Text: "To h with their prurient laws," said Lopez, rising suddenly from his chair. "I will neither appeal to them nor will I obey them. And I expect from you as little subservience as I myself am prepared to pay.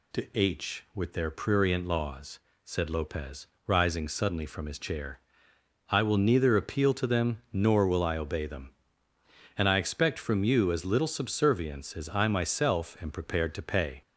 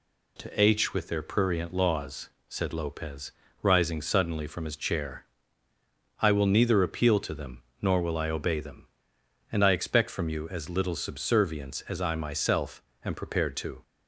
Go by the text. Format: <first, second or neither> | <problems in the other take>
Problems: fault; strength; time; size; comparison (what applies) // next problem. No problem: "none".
first | pauses between "them" and "nor"; slight; at 7.6 s; 0.18 s long // pauses between "myself" and "am"; slight; at 12.8 s; 0.20 s long // stops before "pay"; at 13.8 s